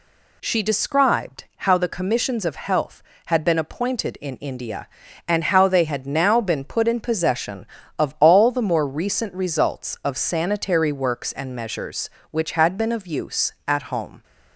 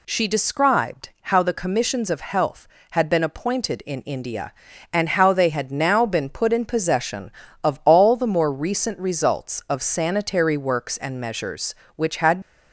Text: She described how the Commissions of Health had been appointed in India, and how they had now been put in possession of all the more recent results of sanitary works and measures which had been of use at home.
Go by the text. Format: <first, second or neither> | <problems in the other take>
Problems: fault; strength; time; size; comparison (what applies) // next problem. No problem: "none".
first | stops before "been of use at home"; at 12.4 s